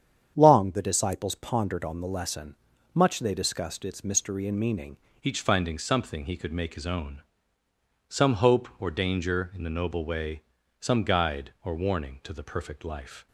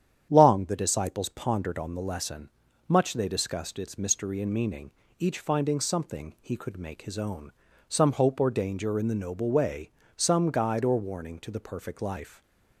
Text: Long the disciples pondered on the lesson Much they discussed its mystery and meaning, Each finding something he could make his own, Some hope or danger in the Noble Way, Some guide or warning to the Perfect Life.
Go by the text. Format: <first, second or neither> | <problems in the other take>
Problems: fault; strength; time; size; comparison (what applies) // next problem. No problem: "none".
second | starts louder than the rest; strong; until 1.3 s; 8 dB; strong in the second // pauses between "lesson" and "Much"; at 2.5 s; 0.38 s long; also in the second // changes voice at "Each"; from 5.2 s on; 8.0 s long